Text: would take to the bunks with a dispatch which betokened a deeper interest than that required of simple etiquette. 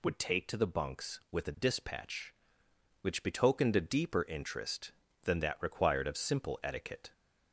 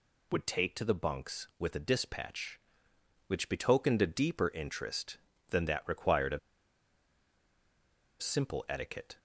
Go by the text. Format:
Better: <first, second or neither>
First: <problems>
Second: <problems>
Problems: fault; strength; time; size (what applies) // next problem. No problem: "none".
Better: first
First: none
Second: pauses between "of" and "simple"; strong; at 6.3 s; 1.8 s long